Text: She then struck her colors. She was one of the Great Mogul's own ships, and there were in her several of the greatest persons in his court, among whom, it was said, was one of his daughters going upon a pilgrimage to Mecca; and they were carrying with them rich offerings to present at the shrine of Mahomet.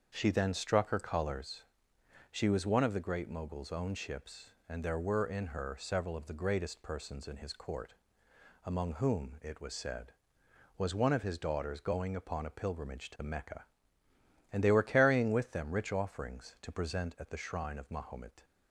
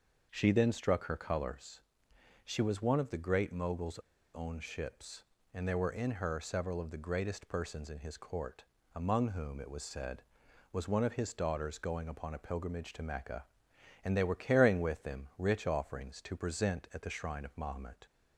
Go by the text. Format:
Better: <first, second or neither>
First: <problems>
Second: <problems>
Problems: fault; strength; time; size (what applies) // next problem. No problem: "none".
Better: first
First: starts louder than the rest; until 1.1 s; 7 dB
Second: starts louder than the rest; noticeable; until 1.3 s; 6 dB // pauses between "Mogul's" and "own"; at 3.9 s; 0.36 s long